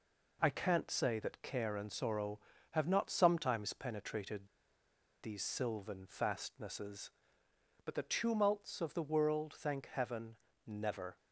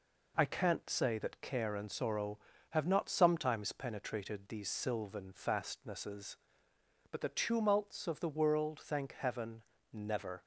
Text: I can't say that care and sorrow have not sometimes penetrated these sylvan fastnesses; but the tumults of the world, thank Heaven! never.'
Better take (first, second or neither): second